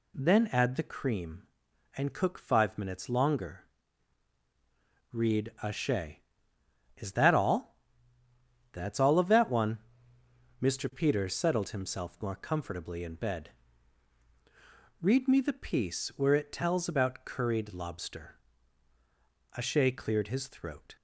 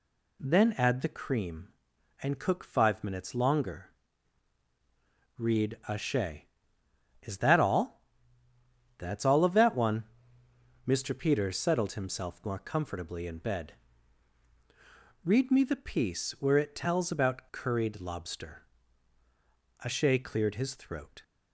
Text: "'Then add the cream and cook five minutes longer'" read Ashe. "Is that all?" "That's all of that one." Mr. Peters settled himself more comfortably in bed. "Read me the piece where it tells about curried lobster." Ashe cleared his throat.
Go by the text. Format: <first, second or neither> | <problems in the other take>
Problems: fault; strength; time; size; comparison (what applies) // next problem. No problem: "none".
neither | pauses between "longer" and "read"; strong; the same in both